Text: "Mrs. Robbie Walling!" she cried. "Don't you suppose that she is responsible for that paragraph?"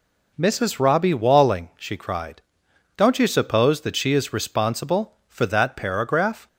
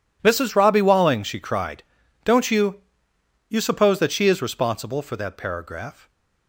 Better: first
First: none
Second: says "you" twice; at 3.4 s

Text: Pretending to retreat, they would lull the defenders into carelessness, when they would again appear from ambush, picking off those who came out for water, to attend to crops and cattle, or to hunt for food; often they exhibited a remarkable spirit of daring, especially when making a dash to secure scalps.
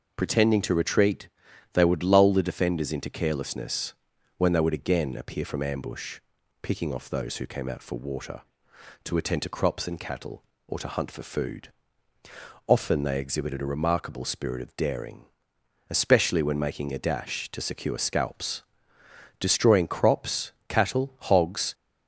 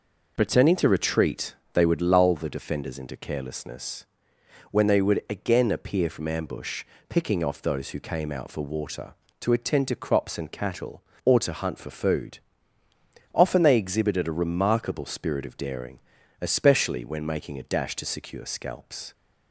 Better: second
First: goes on to say "Destroying crops cattle hogs"; strong; from 19.3 s on; 2.3 s long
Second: none

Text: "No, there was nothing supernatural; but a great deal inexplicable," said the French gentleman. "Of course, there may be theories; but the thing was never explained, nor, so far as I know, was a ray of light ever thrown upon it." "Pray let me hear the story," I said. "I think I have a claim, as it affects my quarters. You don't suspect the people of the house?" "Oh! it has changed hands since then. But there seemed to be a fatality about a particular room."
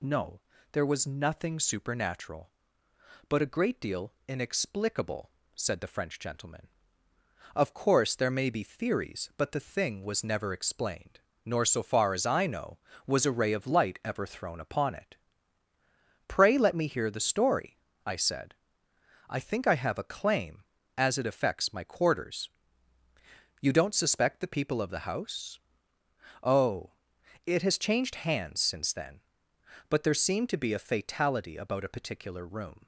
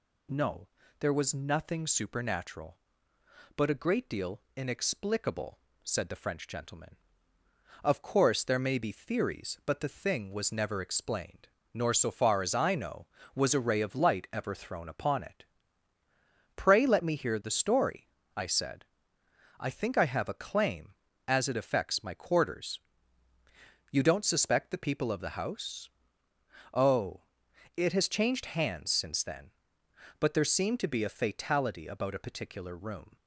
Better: neither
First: pauses between "deal" and "inexplicable"; slight; at 4.1 s; 0.16 s long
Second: pauses between "deal" and "inexplicable"; slight; at 4.3 s; 0.16 s long

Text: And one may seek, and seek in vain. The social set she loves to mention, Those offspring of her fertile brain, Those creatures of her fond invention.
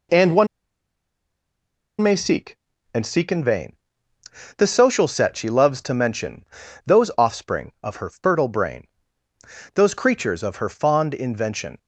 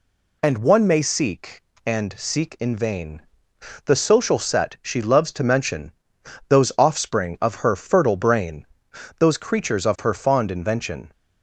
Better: second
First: pauses between "one" and "may"; strong; at 0.4 s; 1.5 s long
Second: none

